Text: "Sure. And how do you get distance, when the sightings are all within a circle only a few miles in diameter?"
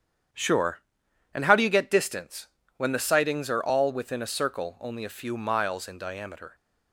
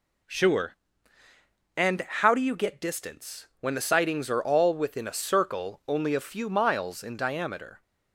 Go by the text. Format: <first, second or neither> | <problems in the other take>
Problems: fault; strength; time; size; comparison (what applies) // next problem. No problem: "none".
second | gets quieter; strong; throughout; 8 dB